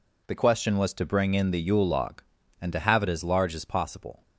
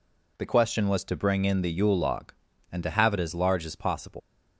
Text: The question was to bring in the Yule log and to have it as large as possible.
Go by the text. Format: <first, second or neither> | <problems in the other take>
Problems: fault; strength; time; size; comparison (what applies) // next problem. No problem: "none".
first | leaves "possible" unfinished; at 4.1 s; 125 ms